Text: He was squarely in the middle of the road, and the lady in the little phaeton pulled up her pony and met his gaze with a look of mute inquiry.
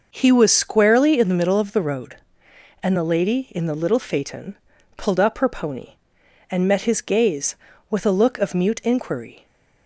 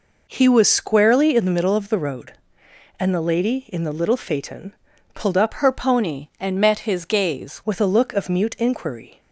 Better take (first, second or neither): first